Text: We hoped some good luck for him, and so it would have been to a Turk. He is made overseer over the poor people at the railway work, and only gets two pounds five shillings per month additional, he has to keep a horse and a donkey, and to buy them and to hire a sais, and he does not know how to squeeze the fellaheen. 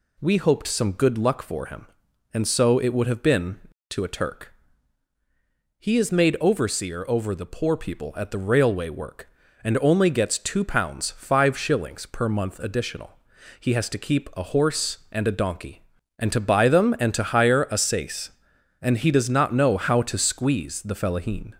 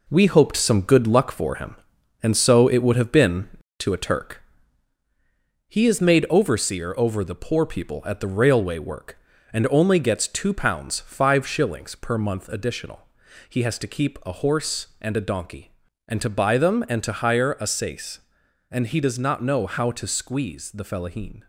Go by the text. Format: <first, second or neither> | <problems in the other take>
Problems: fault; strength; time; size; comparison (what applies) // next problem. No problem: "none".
first | gets quieter; throughout; 6.5 dB